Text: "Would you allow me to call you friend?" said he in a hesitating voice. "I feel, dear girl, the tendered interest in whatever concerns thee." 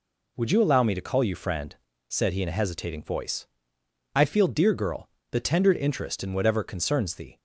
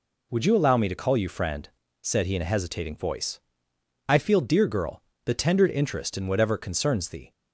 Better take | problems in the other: neither | none

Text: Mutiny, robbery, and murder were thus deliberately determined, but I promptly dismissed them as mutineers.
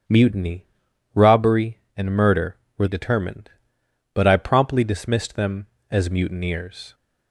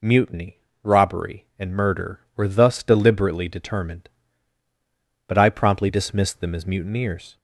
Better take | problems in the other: second | starts louder than the rest; strong; until 1.5 s; 10 dB // skips "thus deliberately"; at 2.8 s

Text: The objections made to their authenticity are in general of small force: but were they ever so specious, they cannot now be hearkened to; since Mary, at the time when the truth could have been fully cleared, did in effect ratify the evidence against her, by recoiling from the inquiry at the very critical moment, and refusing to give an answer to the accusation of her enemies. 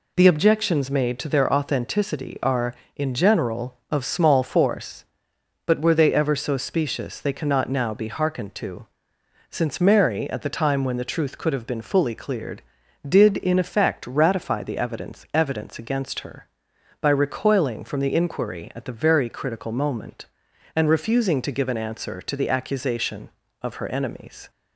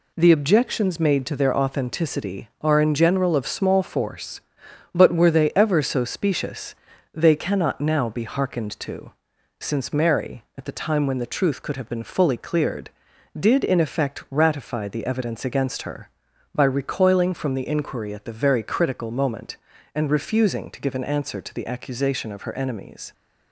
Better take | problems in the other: second | says "evidence" twice; at 15.3 s

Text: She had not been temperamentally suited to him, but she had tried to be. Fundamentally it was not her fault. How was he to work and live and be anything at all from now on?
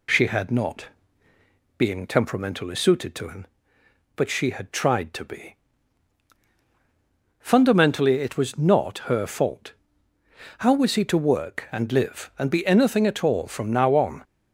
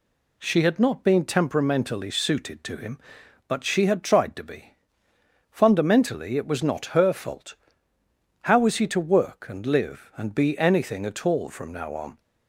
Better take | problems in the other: second | says "being" for "been"; at 1.7 s

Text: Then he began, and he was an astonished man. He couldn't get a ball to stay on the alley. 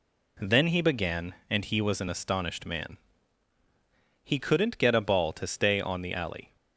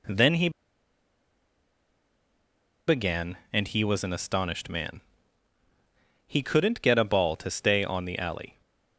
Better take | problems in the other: first | pauses between "he" and "began"; strong; at 0.4 s; 2.3 s long

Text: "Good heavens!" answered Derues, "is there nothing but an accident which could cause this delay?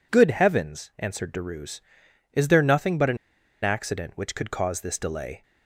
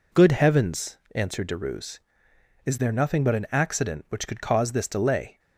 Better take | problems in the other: second | pauses between "an" and "accident"; noticeable; at 3.1 s; 0.46 s long

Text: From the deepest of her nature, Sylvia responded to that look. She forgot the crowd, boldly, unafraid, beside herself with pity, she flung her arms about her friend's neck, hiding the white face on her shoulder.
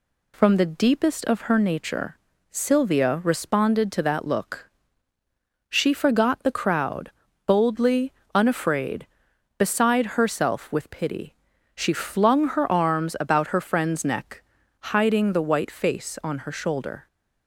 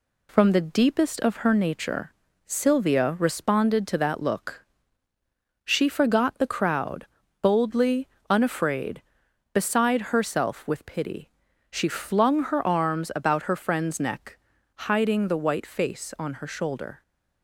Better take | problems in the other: first | gets quieter; slight; throughout; 2.5 dB

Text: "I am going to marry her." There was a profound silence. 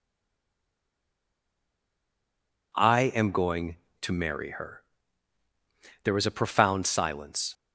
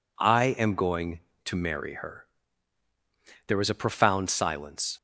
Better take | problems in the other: second | stays silent before the first word; strong; until 2.7 s; 2.7 s long

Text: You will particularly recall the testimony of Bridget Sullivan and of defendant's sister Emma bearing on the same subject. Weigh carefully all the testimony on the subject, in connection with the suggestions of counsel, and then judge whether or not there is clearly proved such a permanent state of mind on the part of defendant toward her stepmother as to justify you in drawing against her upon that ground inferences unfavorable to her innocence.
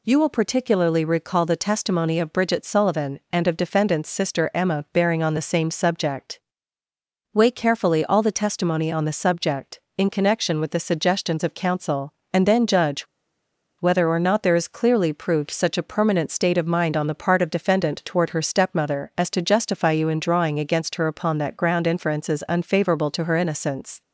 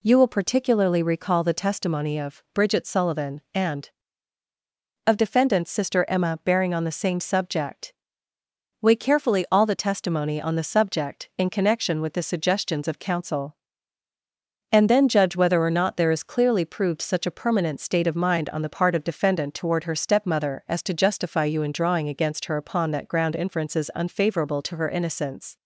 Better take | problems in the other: second | pauses between "judge" and "whether"; noticeable; at 13.0 s; 0.74 s long

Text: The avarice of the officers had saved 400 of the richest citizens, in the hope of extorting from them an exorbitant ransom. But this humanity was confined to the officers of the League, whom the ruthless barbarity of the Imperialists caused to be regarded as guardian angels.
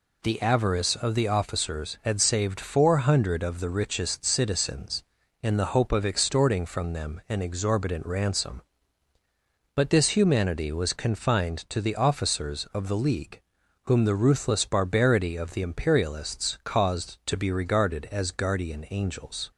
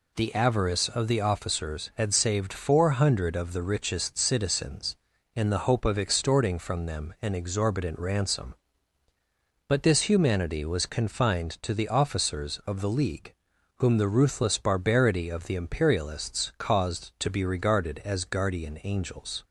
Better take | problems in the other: neither | none

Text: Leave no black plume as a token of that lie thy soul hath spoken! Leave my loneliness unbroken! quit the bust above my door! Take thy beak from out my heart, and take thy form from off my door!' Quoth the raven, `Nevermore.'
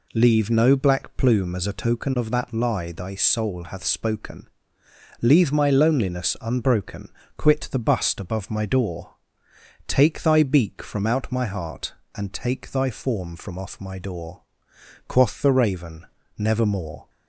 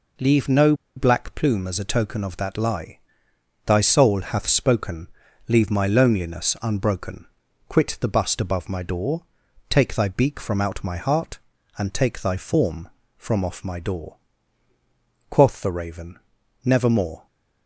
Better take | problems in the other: first | pauses between "no" and "black"; slight; at 0.7 s; 0.22 s long // pauses between "lie" and "thy"; noticeable; at 2.9 s; 0.68 s long

